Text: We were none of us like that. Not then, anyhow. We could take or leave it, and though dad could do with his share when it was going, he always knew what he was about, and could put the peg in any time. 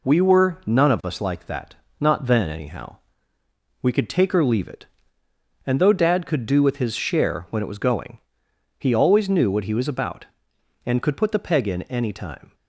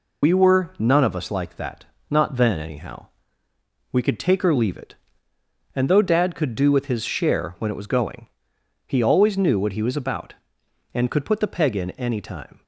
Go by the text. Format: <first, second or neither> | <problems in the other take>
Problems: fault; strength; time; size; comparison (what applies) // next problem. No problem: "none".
first | loses the start of "We"; at 0.2 s; 60 ms